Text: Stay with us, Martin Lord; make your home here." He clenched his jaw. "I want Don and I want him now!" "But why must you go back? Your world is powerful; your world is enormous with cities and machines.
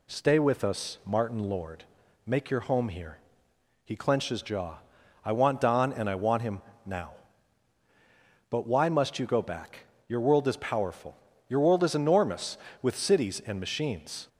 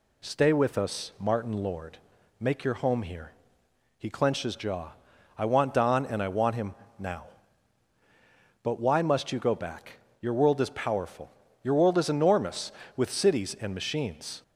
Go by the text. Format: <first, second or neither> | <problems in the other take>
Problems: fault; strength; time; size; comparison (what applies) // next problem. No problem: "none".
neither | pauses between "him" and "now"; slight; the same in both